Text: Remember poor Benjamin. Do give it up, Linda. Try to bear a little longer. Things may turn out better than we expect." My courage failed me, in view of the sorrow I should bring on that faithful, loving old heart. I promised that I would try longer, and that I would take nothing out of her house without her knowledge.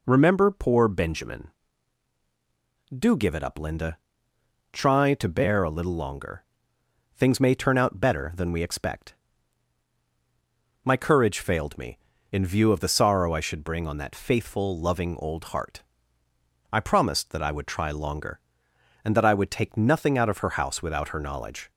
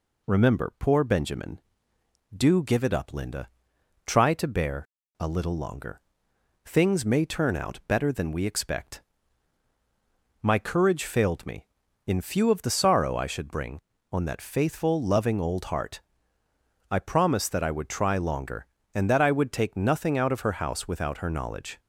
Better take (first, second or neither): first